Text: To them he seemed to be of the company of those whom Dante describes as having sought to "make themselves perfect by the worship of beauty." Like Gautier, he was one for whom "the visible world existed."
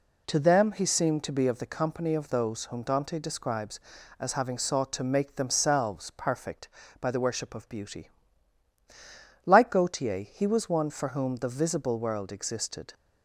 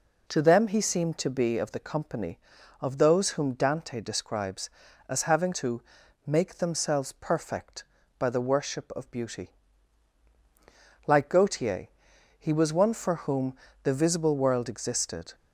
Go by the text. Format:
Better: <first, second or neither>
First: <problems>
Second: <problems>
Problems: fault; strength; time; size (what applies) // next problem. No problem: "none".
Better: first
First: none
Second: skips "sought"; at 5.5 s // pauses between "to" and "make"; at 5.8 s; 0.44 s long // pauses between "whom" and "the"; slight; at 13.5 s; 0.28 s long